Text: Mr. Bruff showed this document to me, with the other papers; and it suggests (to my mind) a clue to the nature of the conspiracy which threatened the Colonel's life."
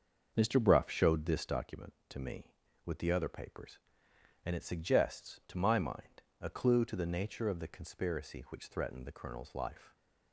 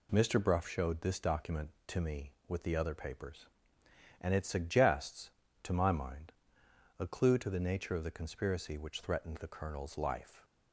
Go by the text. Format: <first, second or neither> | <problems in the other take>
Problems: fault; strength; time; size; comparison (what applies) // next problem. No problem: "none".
second | starts louder than the rest; until 1.7 s; 6.5 dB